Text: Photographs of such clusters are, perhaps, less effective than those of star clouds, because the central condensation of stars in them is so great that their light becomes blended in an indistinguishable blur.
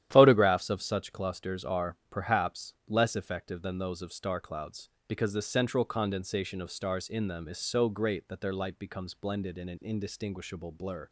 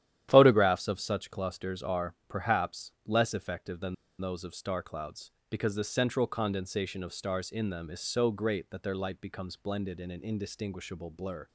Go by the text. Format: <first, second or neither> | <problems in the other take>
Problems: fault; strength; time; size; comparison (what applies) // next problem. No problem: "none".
first | starts louder than the rest; strong; until 1.3 s; 11.5 dB; strong in the first // pauses between "than" and "those"; slight; at 3.9 s; 0.24 s long